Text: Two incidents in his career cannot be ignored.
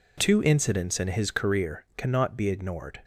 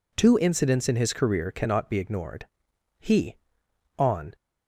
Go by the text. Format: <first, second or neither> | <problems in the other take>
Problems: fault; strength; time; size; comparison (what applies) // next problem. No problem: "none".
first | goes on to say "He on"; from 2.9 s on; 1.3 s long